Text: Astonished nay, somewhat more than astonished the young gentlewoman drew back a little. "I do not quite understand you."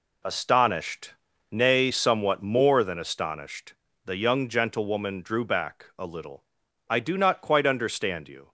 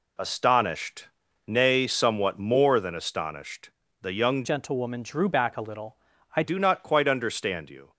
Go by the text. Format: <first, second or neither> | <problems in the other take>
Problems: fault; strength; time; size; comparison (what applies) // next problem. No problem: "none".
first | pauses between "Astonished" and "nay"; at 1.0 s; 0.38 s long; also in the first // pauses between "astonished" and "the"; slight; at 3.6 s; 0.32 s long; slight in the first // changes voice from "gentlewoman" to "I"; from 4.4 to 6.4 s; 2.0 s long